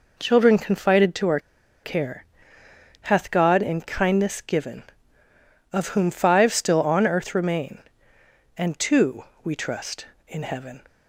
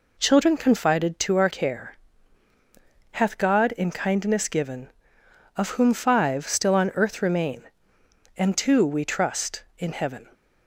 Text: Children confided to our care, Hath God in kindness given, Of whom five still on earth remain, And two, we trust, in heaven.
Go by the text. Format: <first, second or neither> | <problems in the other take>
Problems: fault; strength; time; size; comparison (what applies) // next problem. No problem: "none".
second | pauses between "our" and "care"; at 1.3 s; 0.44 s long